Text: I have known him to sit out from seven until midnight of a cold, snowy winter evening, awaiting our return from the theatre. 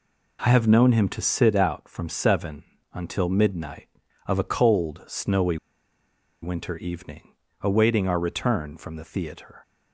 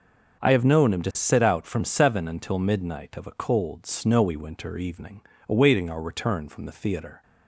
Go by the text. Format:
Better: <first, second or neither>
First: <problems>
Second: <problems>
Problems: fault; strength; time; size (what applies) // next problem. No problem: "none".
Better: second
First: pauses between "seven" and "until"; slight; at 2.6 s; 0.30 s long // pauses between "snowy" and "winter"; noticeable; at 5.5 s; 0.84 s long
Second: none